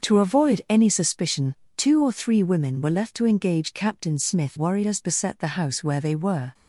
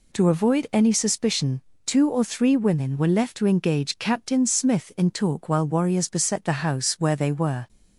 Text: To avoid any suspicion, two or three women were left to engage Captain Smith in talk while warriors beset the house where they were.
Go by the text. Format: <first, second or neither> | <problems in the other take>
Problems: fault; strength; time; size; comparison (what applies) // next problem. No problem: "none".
second | starts louder than the rest; until 1.1 s; 6.5 dB // skips "in talk while"; at 4.5 s